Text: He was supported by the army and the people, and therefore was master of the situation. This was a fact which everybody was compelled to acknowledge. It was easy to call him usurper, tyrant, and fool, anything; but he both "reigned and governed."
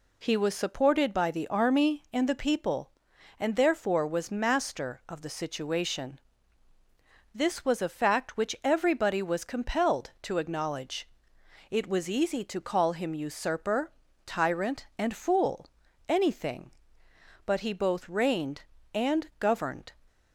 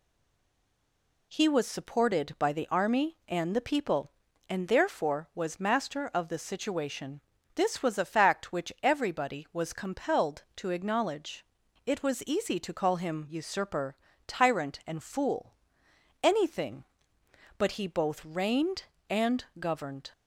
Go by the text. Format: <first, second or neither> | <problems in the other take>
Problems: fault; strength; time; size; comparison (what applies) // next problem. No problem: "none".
first | stays silent before the first word; noticeable; until 1.3 s; 1.3 s long // pauses between "and" and "governed"; slight; at 19.4 s; 0.16 s long